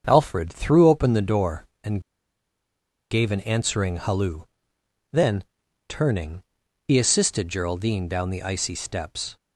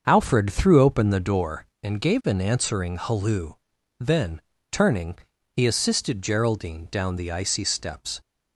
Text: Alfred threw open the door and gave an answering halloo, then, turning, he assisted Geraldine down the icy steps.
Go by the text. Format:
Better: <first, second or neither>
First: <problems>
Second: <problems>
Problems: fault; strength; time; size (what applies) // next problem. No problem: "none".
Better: second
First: starts louder than the rest; until 1.0 s; 7 dB // pauses between "and" and "gave"; at 2.0 s; 1.0 s long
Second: starts louder than the rest; until 1.0 s; 6.5 dB